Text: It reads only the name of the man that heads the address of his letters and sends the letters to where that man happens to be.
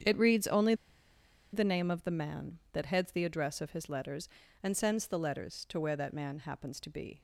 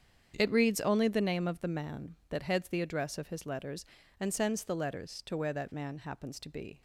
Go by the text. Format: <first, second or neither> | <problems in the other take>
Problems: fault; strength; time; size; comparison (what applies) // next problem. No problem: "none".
second | starts louder than the rest; strong; until 1.8 s; 8 dB; strong in the second // pauses between "only" and "the"; noticeable; at 0.7 s; 0.79 s long